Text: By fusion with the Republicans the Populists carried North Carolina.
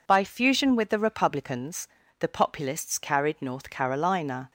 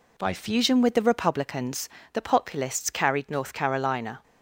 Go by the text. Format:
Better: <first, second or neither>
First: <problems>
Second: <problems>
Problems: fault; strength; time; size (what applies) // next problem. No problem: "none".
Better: neither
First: pauses between "Republicans" and "the"; slight; at 1.8 s; 0.32 s long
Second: pauses between "Republicans" and "the"; slight; at 1.9 s; 0.22 s long